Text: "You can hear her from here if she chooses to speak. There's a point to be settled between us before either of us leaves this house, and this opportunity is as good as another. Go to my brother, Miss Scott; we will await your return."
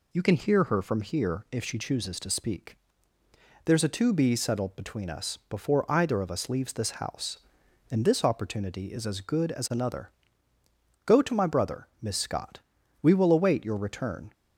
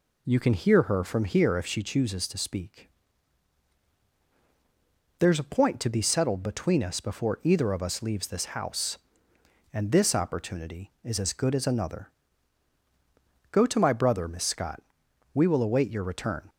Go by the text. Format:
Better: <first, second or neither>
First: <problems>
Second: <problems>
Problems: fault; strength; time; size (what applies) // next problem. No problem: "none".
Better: second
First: skips "point"; at 3.8 s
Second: none